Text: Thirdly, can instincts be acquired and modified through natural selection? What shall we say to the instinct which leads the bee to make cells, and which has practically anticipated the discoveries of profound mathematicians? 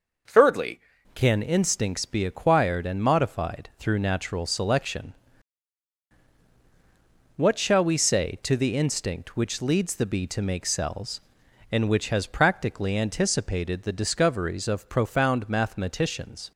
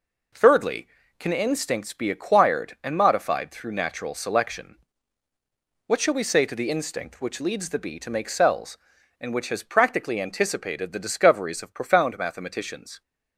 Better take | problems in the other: second | changes voice at "can"; from 1.1 s on; 15.4 s long

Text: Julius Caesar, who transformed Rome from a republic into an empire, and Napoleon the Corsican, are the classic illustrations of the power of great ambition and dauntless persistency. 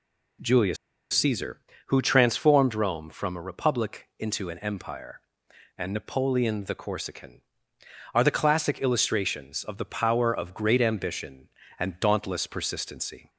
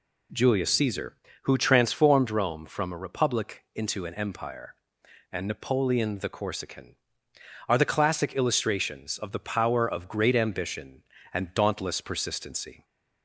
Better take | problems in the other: second | pauses between "Julius" and "Caesar"; at 0.7 s; 0.37 s long

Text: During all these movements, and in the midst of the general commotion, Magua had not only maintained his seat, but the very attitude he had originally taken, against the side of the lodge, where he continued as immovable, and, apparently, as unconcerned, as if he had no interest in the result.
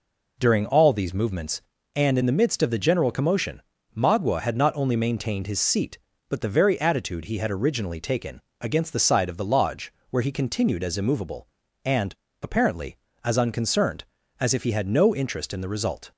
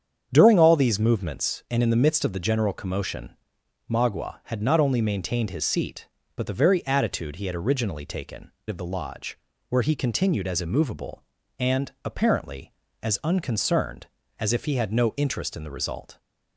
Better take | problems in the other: first | starts louder than the rest; strong; until 1.3 s; 8 dB // skips "against the side"; at 8.5 s

